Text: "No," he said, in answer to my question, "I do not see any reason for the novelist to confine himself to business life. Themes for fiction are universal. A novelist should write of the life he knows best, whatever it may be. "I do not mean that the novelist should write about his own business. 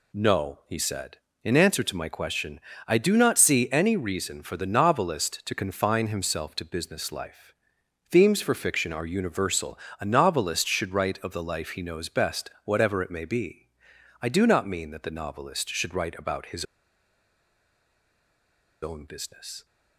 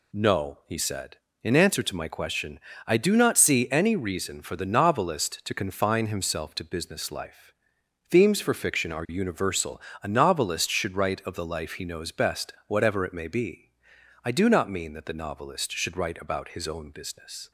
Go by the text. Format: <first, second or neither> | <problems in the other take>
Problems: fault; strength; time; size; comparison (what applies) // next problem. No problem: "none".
second | pauses between "his" and "own"; strong; at 16.6 s; 2.1 s long